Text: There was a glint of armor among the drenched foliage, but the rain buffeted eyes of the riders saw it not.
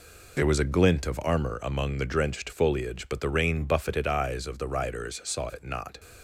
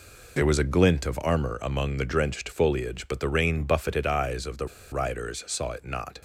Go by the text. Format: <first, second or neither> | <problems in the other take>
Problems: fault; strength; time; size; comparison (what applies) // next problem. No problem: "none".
first | pauses between "the" and "riders"; slight; at 4.6 s; 0.24 s long